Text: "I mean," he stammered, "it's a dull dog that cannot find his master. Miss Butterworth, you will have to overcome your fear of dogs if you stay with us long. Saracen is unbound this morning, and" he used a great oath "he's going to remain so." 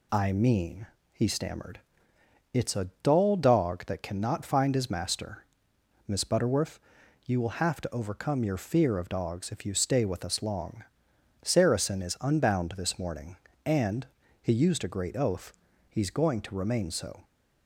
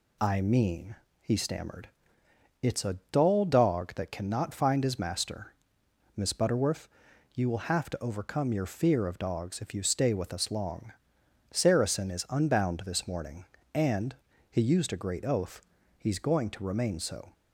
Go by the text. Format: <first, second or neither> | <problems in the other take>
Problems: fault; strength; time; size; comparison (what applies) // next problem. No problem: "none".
neither | pauses between "and" and "he"; slight; the same in both // pauses between "oath" and "he's"; the same in both